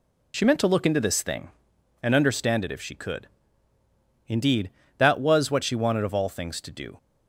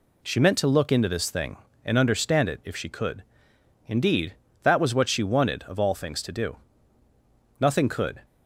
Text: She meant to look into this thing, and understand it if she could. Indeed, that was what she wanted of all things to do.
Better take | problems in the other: first | goes on to say "Nothing could"; noticeable; from 7.5 s on; 0.64 s long

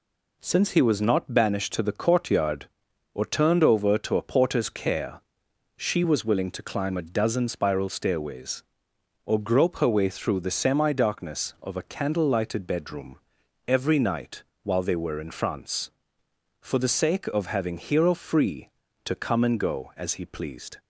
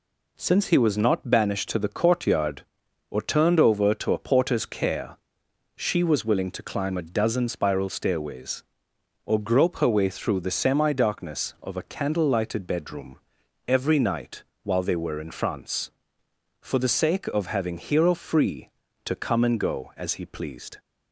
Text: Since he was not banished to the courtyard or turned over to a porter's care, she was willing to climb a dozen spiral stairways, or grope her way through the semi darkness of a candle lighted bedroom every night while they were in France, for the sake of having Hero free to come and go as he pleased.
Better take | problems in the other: neither | pauses between "bedroom" and "every"; noticeable; the same in both // pauses between "night" and "while"; slight; the same in both

